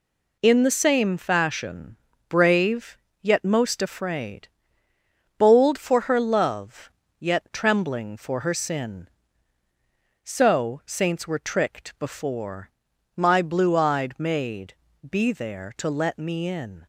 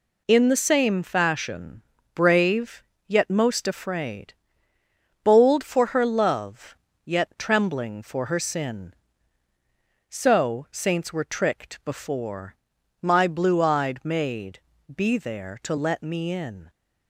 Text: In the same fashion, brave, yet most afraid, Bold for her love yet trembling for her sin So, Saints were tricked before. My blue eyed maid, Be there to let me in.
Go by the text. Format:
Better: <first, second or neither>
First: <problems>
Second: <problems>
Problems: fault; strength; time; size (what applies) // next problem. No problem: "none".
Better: neither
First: pauses between "love" and "yet"; slight; at 6.8 s; 0.30 s long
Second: pauses between "love" and "yet"; slight; at 6.7 s; 0.30 s long